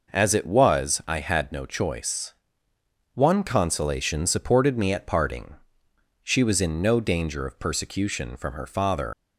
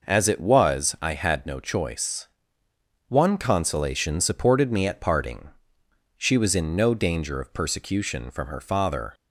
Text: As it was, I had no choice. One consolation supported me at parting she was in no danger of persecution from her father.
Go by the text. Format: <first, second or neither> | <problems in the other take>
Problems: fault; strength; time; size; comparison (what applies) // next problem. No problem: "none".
second | pauses between "parting" and "she"; noticeable; at 5.5 s; 0.68 s long; noticeable in the second // leaves "father" unfinished; at 9.1 s; 65 ms